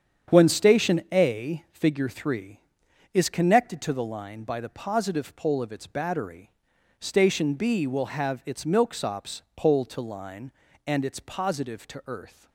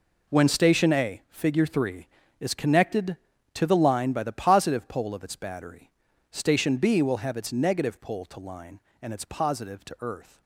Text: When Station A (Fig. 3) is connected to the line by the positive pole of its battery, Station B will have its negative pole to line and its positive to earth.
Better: second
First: starts louder than the rest; strong; until 1.4 s; 8 dB // says "milksops" for "negative"; at 8.6 s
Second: none

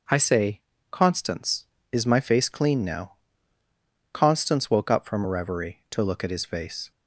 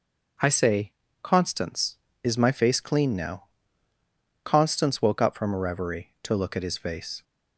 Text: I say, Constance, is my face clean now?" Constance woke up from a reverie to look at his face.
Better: neither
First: none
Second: none

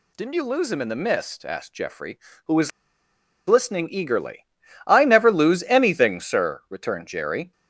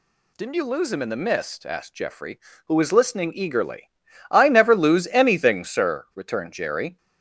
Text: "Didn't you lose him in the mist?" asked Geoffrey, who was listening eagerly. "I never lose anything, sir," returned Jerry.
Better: second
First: pauses between "was" and "listening"; noticeable; at 2.7 s; 0.76 s long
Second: none

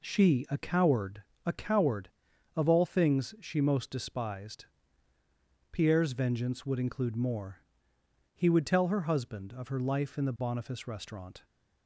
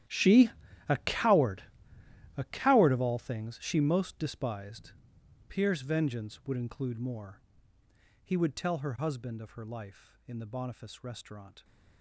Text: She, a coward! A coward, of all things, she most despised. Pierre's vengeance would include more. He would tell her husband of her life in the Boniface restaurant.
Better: first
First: none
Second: gets quieter; strong; throughout; 17.5 dB

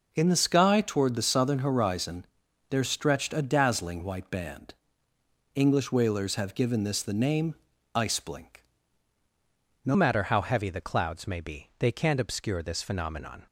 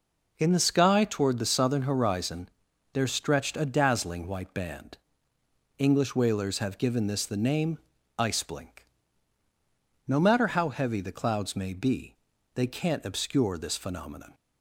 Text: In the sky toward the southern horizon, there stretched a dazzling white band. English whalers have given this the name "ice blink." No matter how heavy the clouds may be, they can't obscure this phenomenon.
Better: second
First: pauses between "name" and "ice"; at 7.5 s; 0.42 s long // changes voice at "matter"; from 9.9 s on; 3.5 s long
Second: pauses between "name" and "ice"; at 7.7 s; 0.42 s long

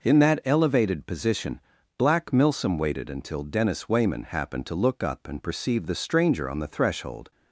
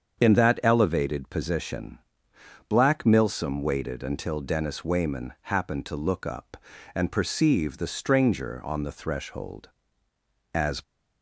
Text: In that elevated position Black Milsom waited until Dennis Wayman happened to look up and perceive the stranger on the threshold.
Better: first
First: pauses between "position" and "Black"; at 1.6 s; 0.38 s long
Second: starts louder than the rest; strong; until 1.2 s; 7 dB // pauses between "position" and "Black"; noticeable; at 1.9 s; 0.68 s long // goes on to say "As"; slight; from 10.5 s on; 0.28 s long

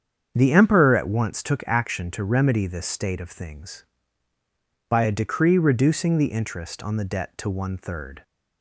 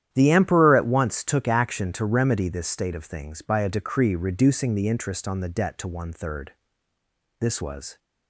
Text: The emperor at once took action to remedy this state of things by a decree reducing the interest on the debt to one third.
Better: first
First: starts louder than the rest; strong; until 1.3 s; 7.5 dB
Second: starts louder than the rest; strong; until 1.1 s; 10.5 dB // goes on to say "This was"; from 7.4 s on; 0.58 s long

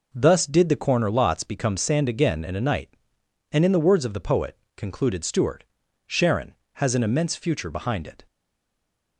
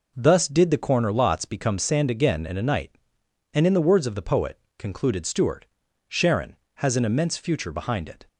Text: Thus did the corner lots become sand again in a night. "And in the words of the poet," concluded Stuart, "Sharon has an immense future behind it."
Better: second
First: stays silent after the last word; slight; from 8.2 s on; 0.9 s long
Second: none

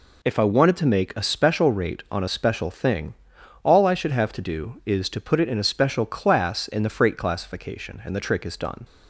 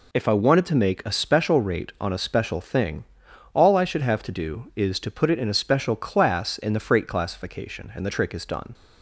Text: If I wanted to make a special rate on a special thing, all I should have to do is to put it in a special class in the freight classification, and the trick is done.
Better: neither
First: none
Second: none

